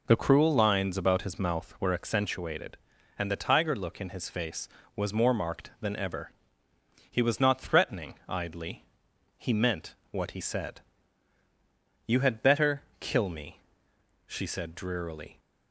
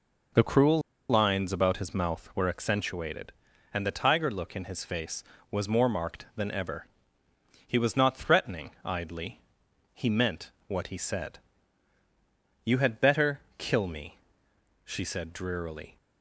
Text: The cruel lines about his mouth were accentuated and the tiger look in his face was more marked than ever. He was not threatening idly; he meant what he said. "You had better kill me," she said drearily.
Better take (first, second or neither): first